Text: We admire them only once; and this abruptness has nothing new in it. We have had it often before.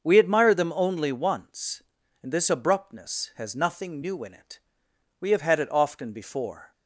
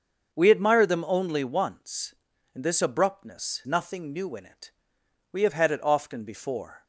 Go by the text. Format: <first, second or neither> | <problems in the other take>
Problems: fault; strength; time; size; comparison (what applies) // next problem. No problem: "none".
first | starts louder than the rest; until 1.3 s; 6.5 dB; also in the first // skips "has"; at 3.6 s